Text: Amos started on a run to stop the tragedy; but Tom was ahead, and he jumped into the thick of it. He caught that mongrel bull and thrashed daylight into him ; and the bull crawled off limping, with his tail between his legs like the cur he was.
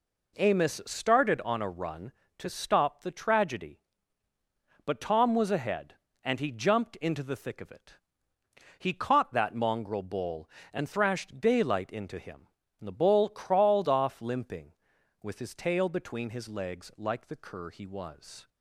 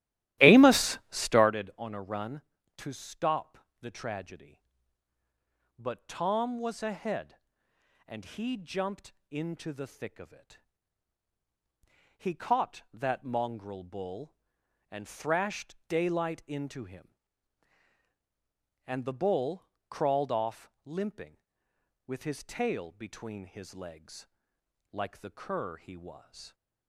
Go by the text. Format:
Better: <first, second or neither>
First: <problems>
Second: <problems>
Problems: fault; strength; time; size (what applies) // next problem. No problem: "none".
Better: first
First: none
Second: starts louder than the rest; strong; until 1.5 s; 14.5 dB // pauses between "stop" and "the"; slight; at 3.5 s; 0.22 s long // pauses between "jumped" and "into"; slight; at 9.1 s; 0.20 s long // pauses between "bull" and "crawled"; slight; at 19.6 s; 0.24 s long // pauses between "legs" and "like"; noticeable; at 24.2 s; 0.64 s long